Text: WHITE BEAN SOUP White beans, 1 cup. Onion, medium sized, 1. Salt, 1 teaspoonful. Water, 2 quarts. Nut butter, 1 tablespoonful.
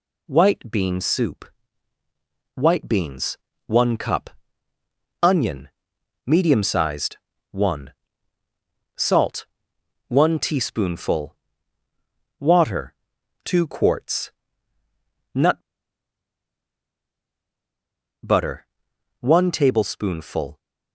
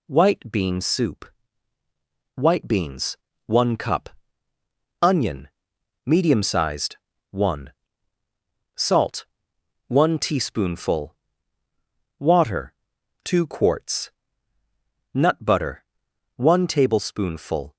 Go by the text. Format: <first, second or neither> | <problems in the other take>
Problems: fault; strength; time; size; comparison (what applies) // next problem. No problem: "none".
second | pauses between "SOUP" and "White"; at 1.4 s; 1.1 s long; also in the second // pauses between "Nut" and "butter"; strong; at 15.6 s; 2.6 s long